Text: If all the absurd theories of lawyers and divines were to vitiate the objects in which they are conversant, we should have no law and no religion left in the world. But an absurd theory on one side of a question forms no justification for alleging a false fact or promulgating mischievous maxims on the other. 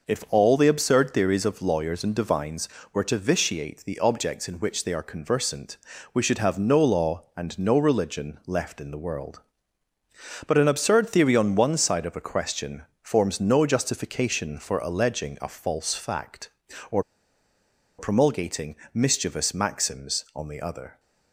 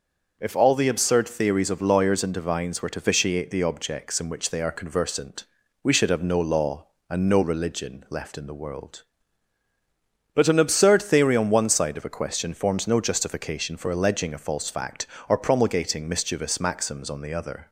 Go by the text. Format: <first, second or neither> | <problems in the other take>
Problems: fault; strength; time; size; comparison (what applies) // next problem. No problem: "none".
second | pauses between "question" and "forms"; slight; at 12.8 s; 0.20 s long // pauses between "or" and "promulgating"; noticeable; at 17.0 s; 0.96 s long // pauses between "promulgating" and "mischievous"; slight; at 18.7 s; 0.18 s long